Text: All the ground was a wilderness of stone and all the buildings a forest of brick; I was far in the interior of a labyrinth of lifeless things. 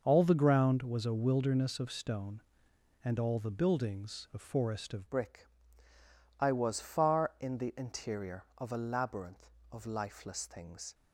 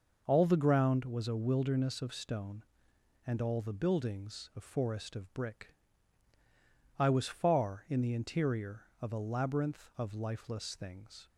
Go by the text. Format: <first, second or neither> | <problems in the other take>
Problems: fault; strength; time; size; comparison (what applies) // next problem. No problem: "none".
second | changes voice at "brick"; from 5.1 s on; 5.8 s long